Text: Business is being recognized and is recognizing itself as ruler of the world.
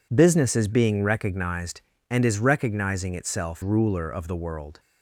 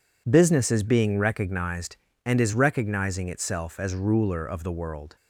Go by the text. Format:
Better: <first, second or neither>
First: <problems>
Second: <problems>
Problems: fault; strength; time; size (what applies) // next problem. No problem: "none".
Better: second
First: skips "as"; at 3.6 s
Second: none